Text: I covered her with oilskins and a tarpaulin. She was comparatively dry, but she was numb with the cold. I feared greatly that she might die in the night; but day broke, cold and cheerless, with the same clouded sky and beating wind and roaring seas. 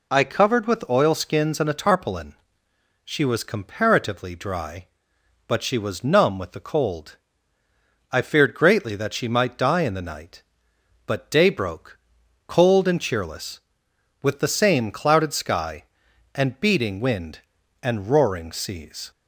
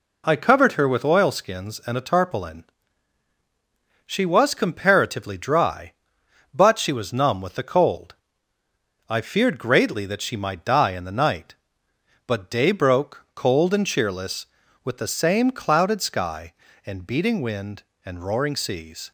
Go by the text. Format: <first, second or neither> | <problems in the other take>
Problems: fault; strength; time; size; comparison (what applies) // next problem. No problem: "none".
second | skips "her"; at 0.6 s